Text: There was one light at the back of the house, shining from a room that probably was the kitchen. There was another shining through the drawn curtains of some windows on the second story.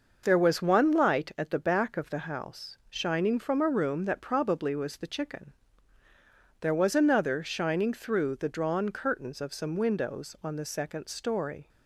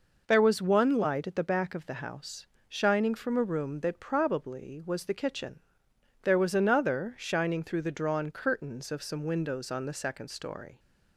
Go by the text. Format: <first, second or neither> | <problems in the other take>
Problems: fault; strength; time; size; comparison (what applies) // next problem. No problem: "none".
second | says "chicken" for "kitchen"; at 5.0 s